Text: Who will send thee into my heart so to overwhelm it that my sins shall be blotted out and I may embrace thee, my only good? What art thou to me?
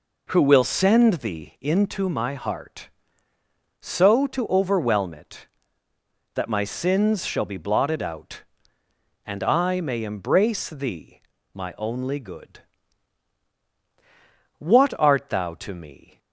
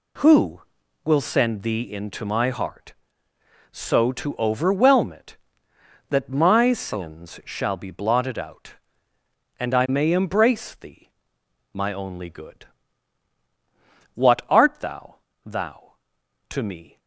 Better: first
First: none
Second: says "thou" twice; at 15.4 s

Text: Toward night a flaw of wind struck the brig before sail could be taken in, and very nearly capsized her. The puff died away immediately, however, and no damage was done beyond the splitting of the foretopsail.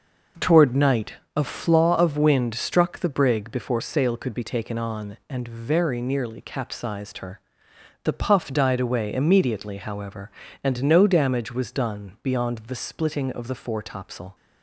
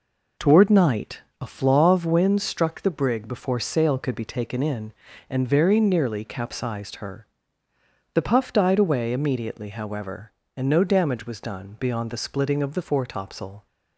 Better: second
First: pauses between "night" and "a"; slight; at 1.1 s; 0.20 s long // says "on" for "in"; at 4.7 s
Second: pauses between "night" and "a"; slight; at 1.2 s; 0.20 s long

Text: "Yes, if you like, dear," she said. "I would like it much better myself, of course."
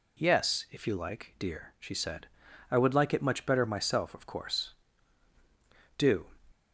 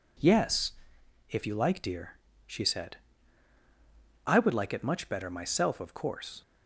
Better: second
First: goes on to say "Do"; slight; from 5.9 s on; 0.36 s long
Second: none

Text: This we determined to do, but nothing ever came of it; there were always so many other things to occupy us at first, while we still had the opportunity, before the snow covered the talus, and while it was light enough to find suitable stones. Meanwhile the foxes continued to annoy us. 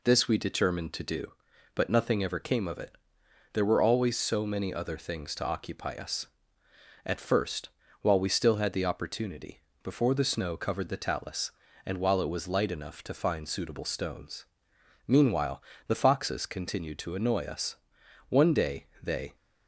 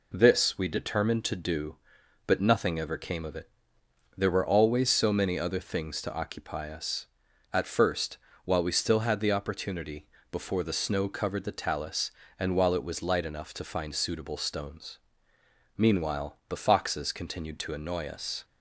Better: second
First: pauses between "Meanwhile" and "the"; slight; at 15.6 s; 0.26 s long // goes on to say "One day they"; noticeable; from 18.2 s on; 1.0 s long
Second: none

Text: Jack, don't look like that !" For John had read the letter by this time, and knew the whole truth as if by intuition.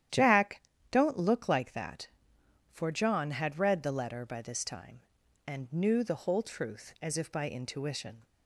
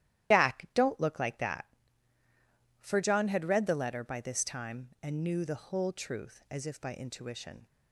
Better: first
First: starts louder than the rest; strong; until 1.4 s; 11 dB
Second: loses the start of "Jack"; at 0.3 s; 100 ms // starts louder than the rest; strong; until 1.3 s; 12 dB

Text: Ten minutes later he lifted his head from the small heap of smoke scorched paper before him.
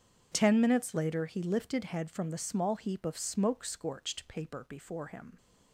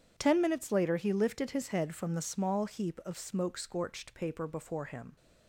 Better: second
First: starts louder than the rest; strong; until 1.3 s; 8 dB // skips "his"; at 1.8 s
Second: none

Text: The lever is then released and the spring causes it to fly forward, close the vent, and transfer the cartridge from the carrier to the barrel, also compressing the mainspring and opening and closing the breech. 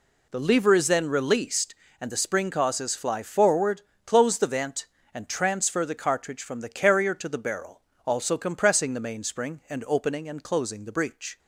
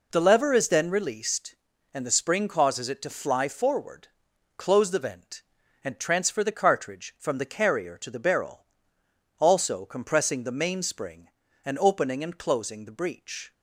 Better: second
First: skips "it to"; at 2.9 s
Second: none

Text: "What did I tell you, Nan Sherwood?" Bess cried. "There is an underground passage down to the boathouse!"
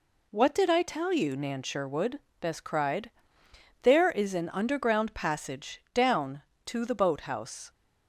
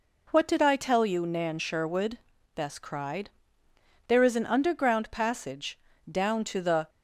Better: first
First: none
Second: pauses between "passage" and "down"; slight; at 5.7 s; 0.32 s long // stops before "boathouse"; at 6.8 s

